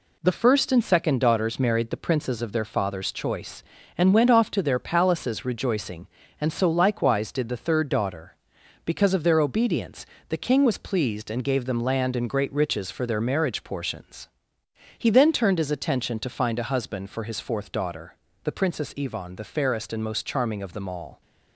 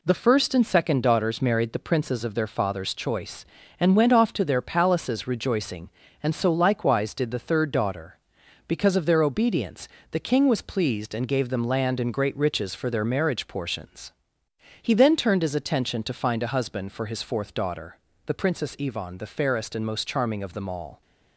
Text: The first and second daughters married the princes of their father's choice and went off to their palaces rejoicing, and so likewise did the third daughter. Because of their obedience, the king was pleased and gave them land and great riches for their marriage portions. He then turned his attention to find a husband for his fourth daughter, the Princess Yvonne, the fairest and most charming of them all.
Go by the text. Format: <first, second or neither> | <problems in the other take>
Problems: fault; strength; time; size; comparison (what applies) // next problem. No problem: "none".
neither | none